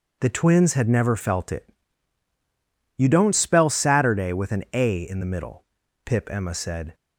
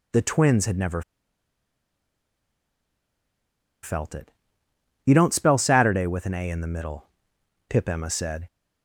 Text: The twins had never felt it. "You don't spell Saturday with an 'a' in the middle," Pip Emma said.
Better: first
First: none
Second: pauses between "never" and "felt"; strong; at 1.0 s; 2.8 s long

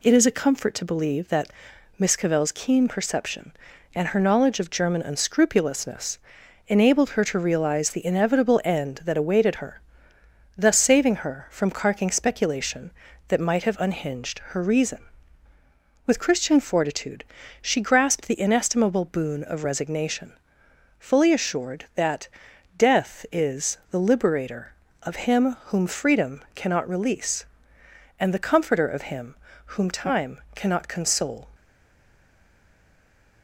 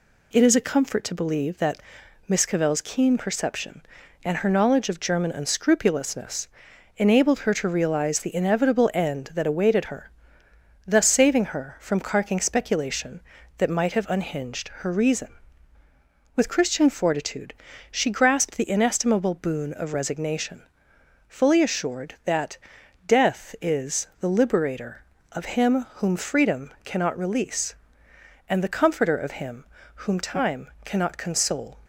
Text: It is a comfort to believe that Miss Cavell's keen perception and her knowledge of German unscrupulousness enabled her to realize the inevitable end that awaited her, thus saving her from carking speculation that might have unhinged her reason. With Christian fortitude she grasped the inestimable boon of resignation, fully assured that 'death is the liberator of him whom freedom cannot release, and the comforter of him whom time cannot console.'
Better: second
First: pauses between "that" and "Miss"; noticeable; at 1.5 s; 0.48 s long // pauses between "unscrupulousness" and "enabled"; noticeable; at 6.1 s; 0.50 s long // pauses between "fortitude" and "she"; at 17.2 s; 0.38 s long // pauses between "that" and "death"; noticeable; at 22.2 s; 0.48 s long // pauses between "him" and "whom"; slight; at 29.3 s; 0.30 s long // stays silent after the last word; noticeable; from 31.5 s on; 1.9 s long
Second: pauses between "that" and "Miss"; noticeable; at 1.8 s; 0.48 s long // pauses between "unscrupulousness" and "enabled"; noticeable; at 6.4 s; 0.50 s long // pauses between "fortitude" and "she"; at 17.5 s; 0.38 s long // pauses between "that" and "death"; noticeable; at 22.5 s; 0.48 s long // pauses between "him" and "whom"; slight; at 29.6 s; 0.30 s long

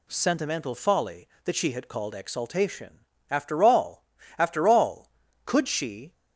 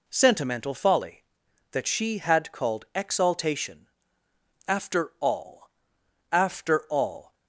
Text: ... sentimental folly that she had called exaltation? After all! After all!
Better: second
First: goes on to say "Could she"; noticeable; from 5.4 s on; 0.68 s long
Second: none

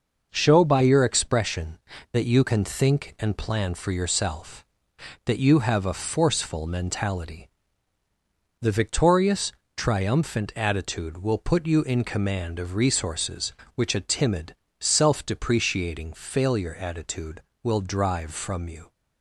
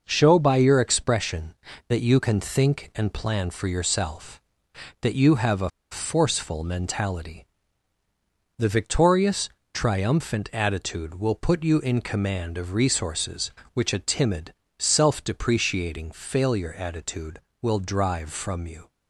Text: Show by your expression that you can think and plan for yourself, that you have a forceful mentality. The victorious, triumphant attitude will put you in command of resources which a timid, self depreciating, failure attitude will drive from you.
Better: first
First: none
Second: pauses between "a" and "forceful"; slight; at 5.6 s; 0.21 s long

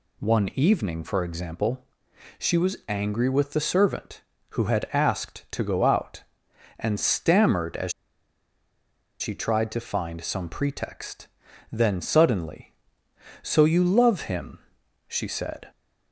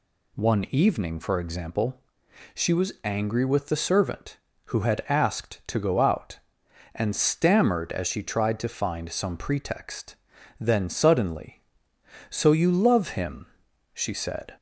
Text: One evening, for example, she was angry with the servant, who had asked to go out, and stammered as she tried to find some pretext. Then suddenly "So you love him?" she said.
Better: second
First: pauses between "as" and "she"; strong; at 7.9 s; 1.2 s long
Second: none

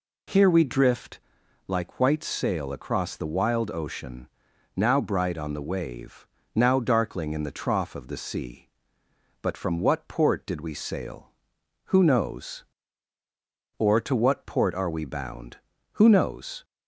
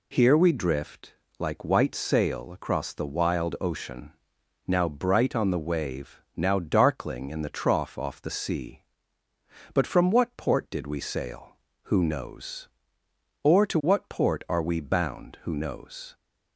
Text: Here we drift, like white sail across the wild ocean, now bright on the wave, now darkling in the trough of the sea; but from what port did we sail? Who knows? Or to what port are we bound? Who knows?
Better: first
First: none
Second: says "off" for "of"; at 7.9 s

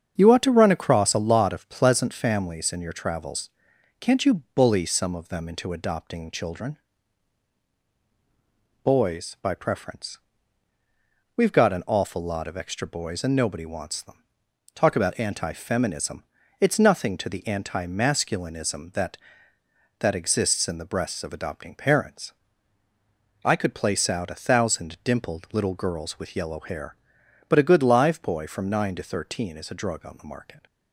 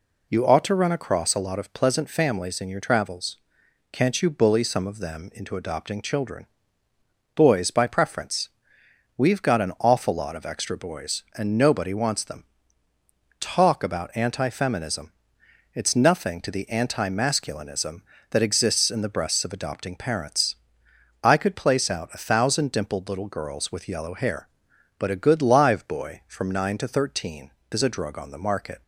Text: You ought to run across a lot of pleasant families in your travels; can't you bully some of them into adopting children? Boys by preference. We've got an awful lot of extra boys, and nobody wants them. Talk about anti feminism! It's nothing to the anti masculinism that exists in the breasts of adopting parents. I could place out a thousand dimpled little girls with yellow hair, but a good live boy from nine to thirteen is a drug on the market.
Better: second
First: starts louder than the rest; strong; until 1.2 s; 7.5 dB // says "that" twice; at 19.9 s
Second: none

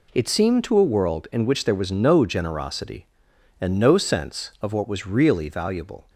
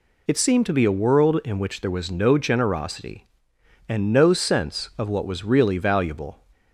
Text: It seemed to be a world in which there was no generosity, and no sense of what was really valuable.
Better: second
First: skips "be"; at 0.7 s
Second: none

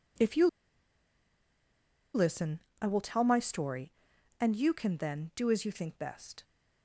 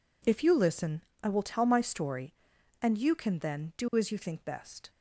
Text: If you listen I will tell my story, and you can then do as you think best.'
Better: second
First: pauses between "you" and "listen"; strong; at 0.4 s; 1.6 s long // pauses between "listen" and "I"; slight; at 2.5 s; 0.20 s long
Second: pauses between "listen" and "I"; slight; at 1.0 s; 0.20 s long

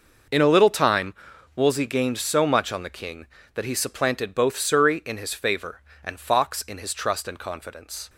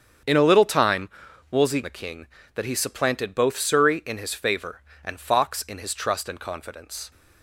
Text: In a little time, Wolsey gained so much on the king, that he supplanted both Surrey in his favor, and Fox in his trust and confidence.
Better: first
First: none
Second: starts louder than the rest; strong; until 1.6 s; 7.5 dB // skips "gained so much on"; at 1.8 s

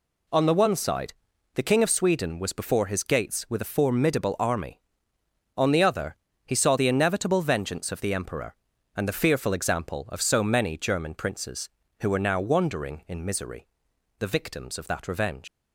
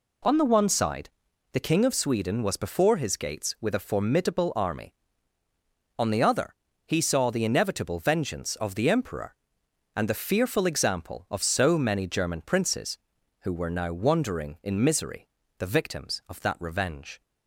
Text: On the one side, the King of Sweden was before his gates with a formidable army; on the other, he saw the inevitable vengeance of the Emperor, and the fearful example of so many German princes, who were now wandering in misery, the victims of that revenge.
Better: second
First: leaves "revenge" unfinished; at 15.4 s; 115 ms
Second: none

